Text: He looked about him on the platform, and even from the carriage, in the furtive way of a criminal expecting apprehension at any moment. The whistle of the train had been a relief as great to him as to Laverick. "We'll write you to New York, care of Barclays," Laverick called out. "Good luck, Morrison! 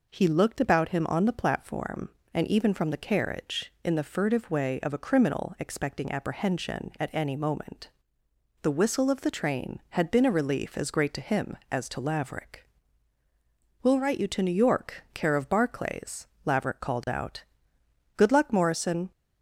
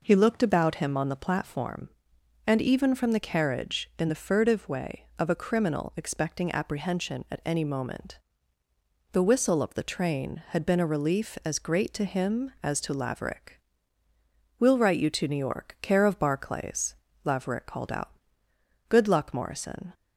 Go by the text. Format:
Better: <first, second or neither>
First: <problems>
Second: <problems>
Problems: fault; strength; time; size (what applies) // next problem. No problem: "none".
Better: neither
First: none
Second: none